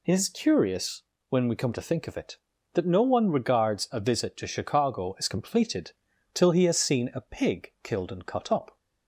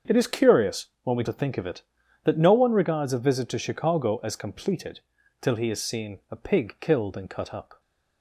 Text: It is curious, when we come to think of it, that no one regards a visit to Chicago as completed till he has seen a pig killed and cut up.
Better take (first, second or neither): first